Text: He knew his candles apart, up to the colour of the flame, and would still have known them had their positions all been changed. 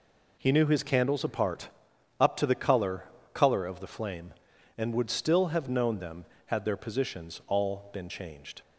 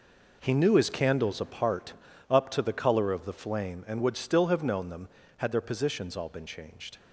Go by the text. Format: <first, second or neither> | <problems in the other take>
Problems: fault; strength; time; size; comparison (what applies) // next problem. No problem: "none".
second | says "colour" twice; at 3.3 s